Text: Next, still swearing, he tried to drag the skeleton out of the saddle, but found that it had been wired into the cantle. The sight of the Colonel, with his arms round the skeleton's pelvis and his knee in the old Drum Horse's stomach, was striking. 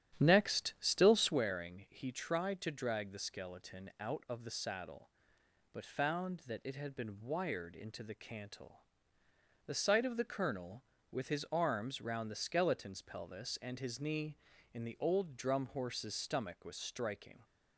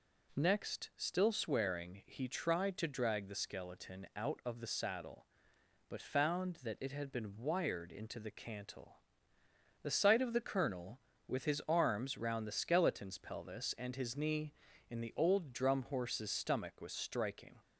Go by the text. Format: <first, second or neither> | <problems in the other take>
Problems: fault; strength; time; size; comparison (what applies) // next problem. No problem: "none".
second | starts louder than the rest; strong; until 1.4 s; 10 dB